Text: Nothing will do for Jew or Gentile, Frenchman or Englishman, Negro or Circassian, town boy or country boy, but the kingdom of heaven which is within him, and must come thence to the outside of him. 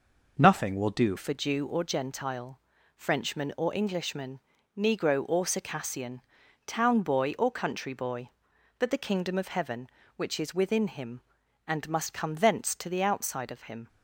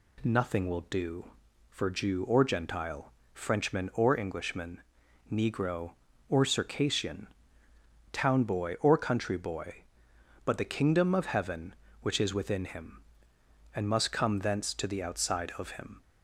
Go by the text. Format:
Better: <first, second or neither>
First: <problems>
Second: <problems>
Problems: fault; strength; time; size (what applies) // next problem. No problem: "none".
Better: second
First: changes voice at "for"; from 1.1 s on; 12.7 s long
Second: none